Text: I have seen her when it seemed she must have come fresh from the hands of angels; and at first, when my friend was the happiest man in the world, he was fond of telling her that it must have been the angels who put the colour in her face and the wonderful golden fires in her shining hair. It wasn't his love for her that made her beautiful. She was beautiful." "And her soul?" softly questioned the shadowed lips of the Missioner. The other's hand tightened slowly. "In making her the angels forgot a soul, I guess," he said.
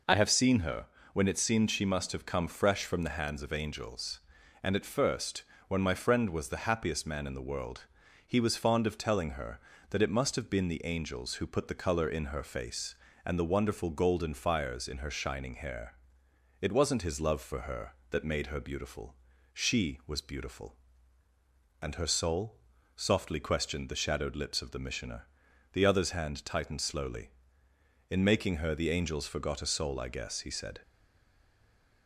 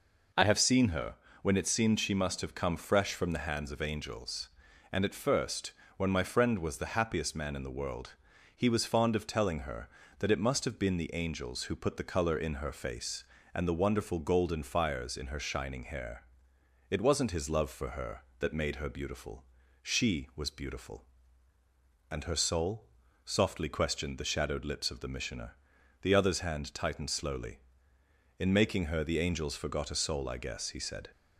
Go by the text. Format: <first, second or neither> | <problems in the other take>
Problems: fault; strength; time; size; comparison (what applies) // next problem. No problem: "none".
second | pauses between "her" and "when"; slight; at 0.8 s; 0.28 s long; slight in the second // stays silent after the last word; noticeable; from 30.8 s on; 1.2 s long